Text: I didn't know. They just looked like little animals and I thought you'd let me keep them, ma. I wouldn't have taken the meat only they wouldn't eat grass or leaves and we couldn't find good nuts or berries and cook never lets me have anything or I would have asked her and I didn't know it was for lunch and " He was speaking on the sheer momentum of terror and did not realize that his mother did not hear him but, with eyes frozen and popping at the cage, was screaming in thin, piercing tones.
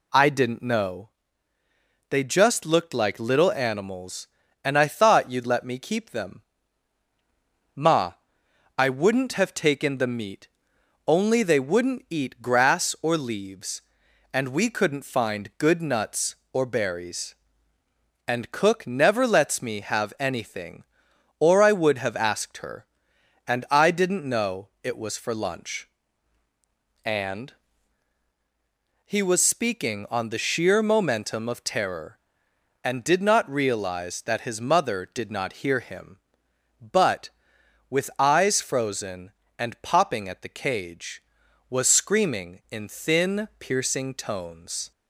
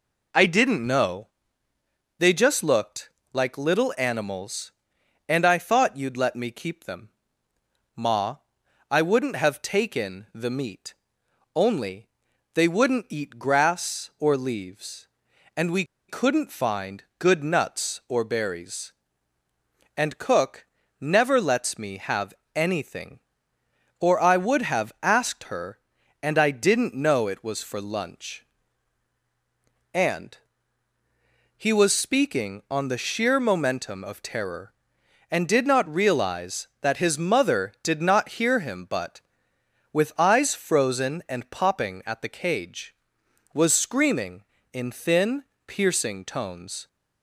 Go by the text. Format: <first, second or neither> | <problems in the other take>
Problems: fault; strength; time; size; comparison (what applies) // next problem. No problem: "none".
first | pauses between "looked" and "like"; slight; at 3.0 s; 0.24 s long // pauses between "meat" and "only"; noticeable; at 10.9 s; 0.62 s long; noticeable in the first // pauses between "only" and "they"; noticeable; at 12.0 s; 0.46 s long // pauses between "we" and "couldn't"; slight; at 15.8 s; 0.25 s long // pauses between "cook" and "never"; slight; at 20.6 s; 0.34 s long // pauses between "have" and "anything"; slight; at 22.3 s; 0.22 s long